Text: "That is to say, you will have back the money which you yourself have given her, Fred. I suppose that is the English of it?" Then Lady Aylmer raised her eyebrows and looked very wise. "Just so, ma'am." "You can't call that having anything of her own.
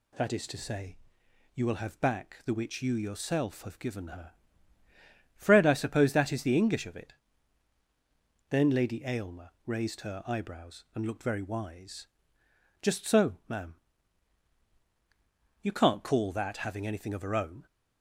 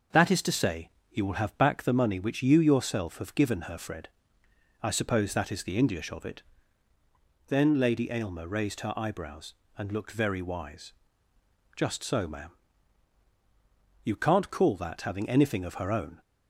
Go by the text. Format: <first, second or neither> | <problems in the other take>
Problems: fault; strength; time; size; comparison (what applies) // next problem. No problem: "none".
second | skips "money"; at 2.5 s // pauses between "Aylmer" and "raised"; slight; at 9.4 s; 0.16 s long